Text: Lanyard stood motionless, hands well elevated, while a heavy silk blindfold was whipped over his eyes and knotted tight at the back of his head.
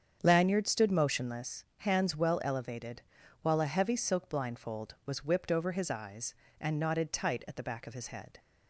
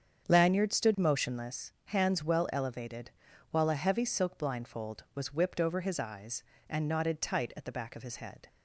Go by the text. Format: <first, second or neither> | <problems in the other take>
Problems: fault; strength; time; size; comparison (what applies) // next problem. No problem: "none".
neither | starts louder than the rest; strong; the same in both